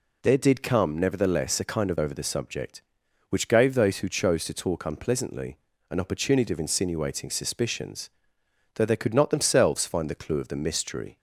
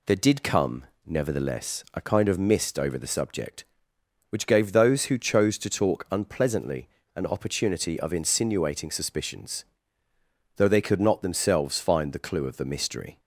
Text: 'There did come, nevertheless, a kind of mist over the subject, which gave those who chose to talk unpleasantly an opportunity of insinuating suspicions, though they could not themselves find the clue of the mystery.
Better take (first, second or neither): second